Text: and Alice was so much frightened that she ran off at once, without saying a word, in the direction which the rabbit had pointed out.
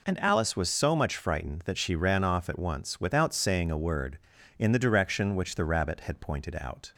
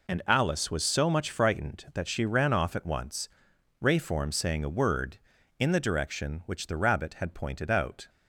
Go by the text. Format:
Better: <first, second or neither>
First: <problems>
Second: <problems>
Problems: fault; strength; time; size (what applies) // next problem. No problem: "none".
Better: first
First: none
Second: says "rayform" for "without"; at 3.8 s